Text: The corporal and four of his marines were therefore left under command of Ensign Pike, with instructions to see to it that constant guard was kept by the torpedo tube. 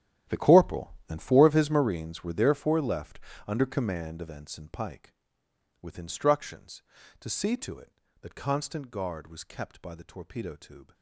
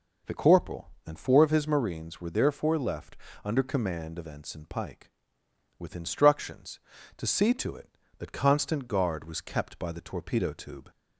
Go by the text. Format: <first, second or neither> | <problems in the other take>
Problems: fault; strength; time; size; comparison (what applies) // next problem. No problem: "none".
second | gets quieter; strong; throughout; 16.5 dB // pauses between "left" and "under"; slight; at 3.1 s; 0.28 s long; slight in the second